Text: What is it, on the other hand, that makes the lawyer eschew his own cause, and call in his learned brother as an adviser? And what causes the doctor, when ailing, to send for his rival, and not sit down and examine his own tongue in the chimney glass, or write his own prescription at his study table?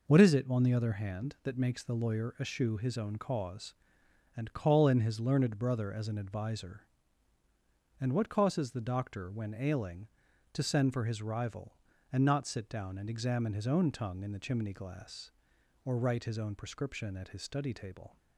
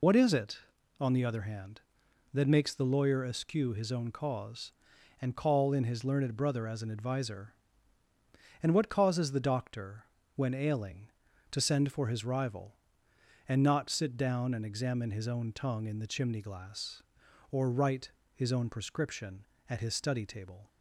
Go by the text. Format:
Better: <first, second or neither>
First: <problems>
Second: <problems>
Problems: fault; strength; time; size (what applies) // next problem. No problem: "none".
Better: first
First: none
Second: loses the start of "What"; at 0.0 s; 65 ms // pauses between "write" and "his"; slight; at 18.0 s; 0.24 s long